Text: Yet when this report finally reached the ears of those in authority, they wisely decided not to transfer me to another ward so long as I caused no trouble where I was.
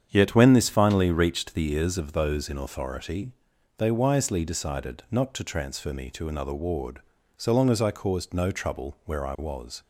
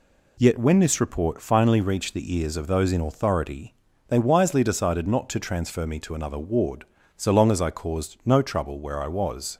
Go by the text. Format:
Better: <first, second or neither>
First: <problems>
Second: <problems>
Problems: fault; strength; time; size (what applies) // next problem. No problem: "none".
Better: second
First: starts louder than the rest; strong; until 1.0 s; 8 dB // skips "report"; at 0.6 s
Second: none